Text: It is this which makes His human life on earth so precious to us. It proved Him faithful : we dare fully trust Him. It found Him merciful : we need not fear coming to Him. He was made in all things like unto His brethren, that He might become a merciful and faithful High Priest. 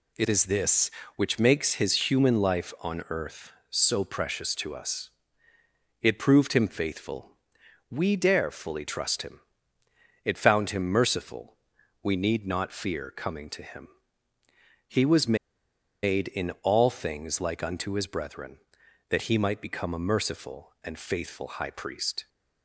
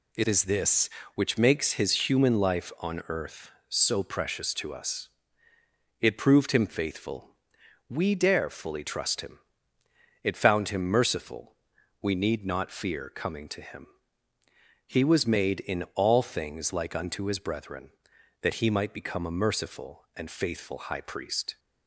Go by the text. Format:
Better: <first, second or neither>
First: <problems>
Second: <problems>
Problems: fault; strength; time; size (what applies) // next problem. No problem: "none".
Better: second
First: pauses between "was" and "made"; noticeable; at 15.3 s; 0.68 s long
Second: none